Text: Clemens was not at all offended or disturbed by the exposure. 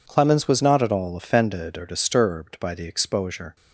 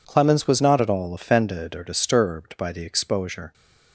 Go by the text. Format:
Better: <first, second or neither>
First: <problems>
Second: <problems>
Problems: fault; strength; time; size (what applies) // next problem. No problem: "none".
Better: neither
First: none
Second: none